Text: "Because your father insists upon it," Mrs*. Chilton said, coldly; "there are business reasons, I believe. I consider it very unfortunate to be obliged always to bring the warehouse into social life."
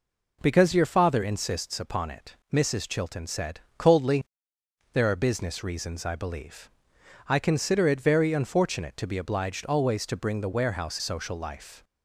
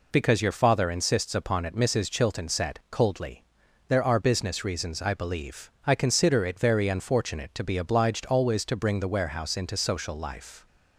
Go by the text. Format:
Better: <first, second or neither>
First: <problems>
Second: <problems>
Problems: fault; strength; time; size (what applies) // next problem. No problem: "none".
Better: second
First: skips "into"; at 10.9 s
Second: none